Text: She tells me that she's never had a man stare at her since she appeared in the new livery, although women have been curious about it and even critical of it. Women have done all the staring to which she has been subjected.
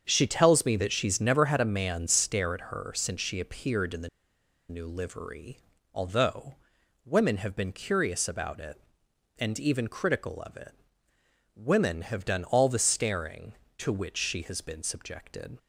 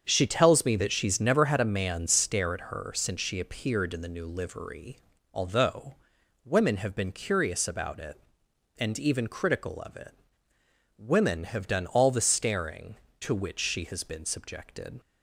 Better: second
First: starts louder than the rest; strong; until 1.0 s; 7 dB // pauses between "the" and "new"; noticeable; at 4.0 s; 0.61 s long // pauses between "although" and "women"; noticeable; at 6.5 s; 0.48 s long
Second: starts louder than the rest; strong; until 1.0 s; 7.5 dB // pauses between "although" and "women"; noticeable; at 5.9 s; 0.48 s long

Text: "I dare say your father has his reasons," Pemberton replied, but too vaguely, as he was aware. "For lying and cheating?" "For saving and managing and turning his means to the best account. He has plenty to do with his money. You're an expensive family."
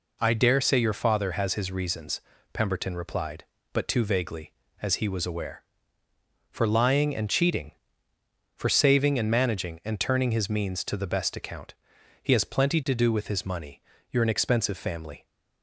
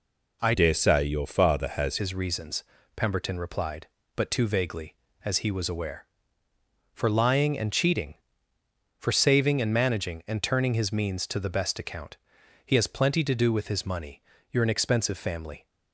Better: first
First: none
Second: changes voice from "dare" to "has"; from 0.5 to 1.9 s; 1.4 s long

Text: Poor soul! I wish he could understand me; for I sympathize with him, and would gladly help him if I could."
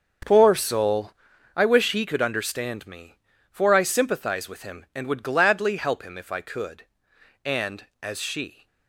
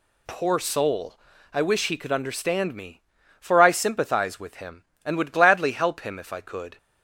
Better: second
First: starts louder than the rest; until 1.7 s; 6.5 dB // goes on to say "And as she"; noticeable; from 7.4 s on; 1.2 s long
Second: none

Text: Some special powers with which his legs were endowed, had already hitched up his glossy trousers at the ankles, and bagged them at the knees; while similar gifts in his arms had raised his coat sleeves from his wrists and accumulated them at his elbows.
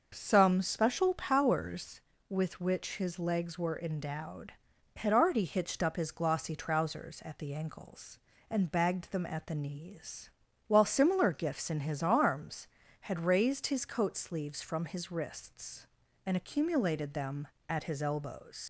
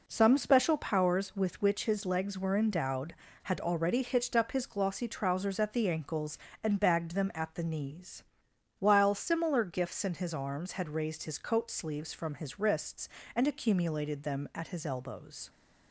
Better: second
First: starts louder than the rest; until 1.1 s; 6 dB // leaves "elbows" unfinished; at 18.6 s; 85 ms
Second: none

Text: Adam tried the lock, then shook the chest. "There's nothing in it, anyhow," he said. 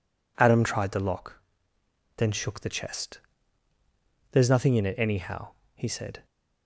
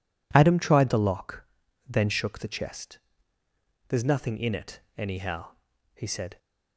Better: neither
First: none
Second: none

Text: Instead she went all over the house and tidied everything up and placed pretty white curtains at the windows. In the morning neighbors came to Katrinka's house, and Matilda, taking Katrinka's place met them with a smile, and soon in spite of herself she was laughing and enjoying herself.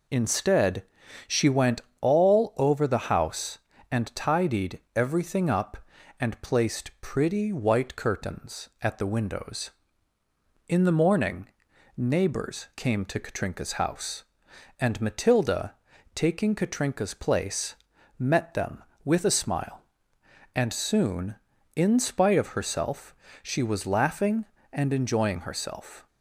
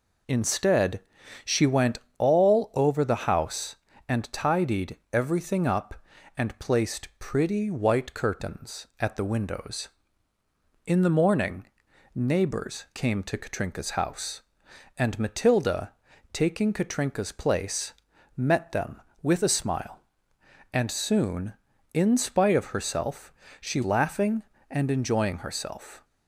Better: first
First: pauses between "Instead" and "she"; at 0.8 s; 0.44 s long // pauses between "went" and "all"; slight; at 1.8 s; 0.18 s long // pauses between "tidied" and "everything"; slight; at 4.7 s; 0.16 s long // pauses between "morning" and "neighbors"; noticeable; at 11.4 s; 0.50 s long // pauses between "place" and "met"; at 17.7 s; 0.44 s long // pauses between "herself" and "she"; slight; at 23.1 s; 0.28 s long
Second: pauses between "Instead" and "she"; at 1.0 s; 0.44 s long // pauses between "went" and "all"; slight; at 1.9 s; 0.18 s long // pauses between "tidied" and "everything"; slight; at 4.9 s; 0.16 s long // pauses between "morning" and "neighbors"; noticeable; at 11.6 s; 0.50 s long // pauses between "place" and "met"; at 17.9 s; 0.44 s long // pauses between "herself" and "she"; slight; at 23.3 s; 0.28 s long // skips "was"; at 23.8 s

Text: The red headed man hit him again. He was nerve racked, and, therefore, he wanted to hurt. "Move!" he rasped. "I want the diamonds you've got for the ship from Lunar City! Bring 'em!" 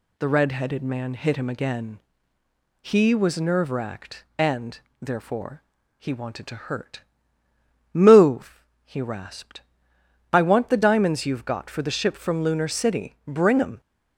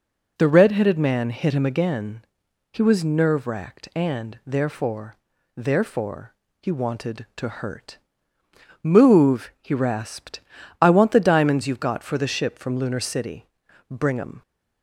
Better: first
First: none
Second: says "therefore" twice; at 5.5 s

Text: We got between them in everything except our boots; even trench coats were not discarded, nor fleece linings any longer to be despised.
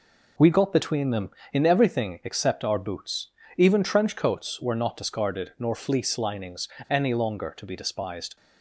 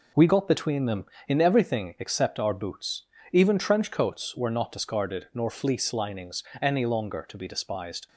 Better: neither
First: pauses between "linings" and "any"; slight; at 6.6 s; 0.21 s long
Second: pauses between "linings" and "any"; slight; at 6.4 s; 0.18 s long

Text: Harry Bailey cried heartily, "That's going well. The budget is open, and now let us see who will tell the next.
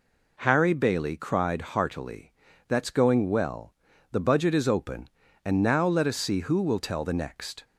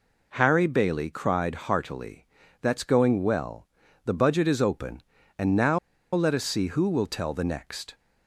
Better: first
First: none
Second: pauses between "now" and "let"; slight; at 5.7 s; 0.35 s long

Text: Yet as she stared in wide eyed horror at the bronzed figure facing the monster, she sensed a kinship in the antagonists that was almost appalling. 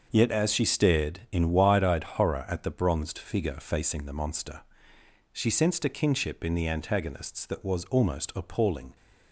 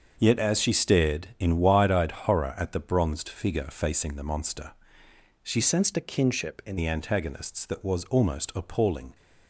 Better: first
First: starts louder than the rest; until 1.1 s; 6.5 dB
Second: starts louder than the rest; until 1.2 s; 6.5 dB // changes voice from "sensed" to "in"; from 5.6 to 6.7 s; 1.1 s long

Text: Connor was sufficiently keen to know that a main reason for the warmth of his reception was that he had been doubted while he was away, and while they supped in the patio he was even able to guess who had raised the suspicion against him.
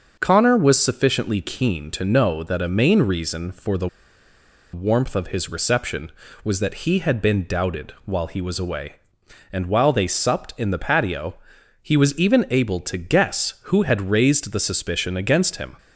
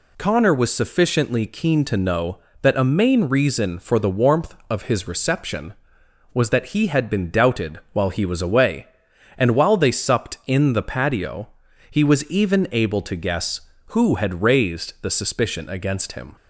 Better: second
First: starts louder than the rest; until 1.2 s; 6.5 dB // pauses between "the" and "warmth"; noticeable; at 3.8 s; 0.85 s long // pauses between "patio" and "he"; noticeable; at 11.3 s; 0.46 s long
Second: pauses between "patio" and "he"; at 11.4 s; 0.41 s long

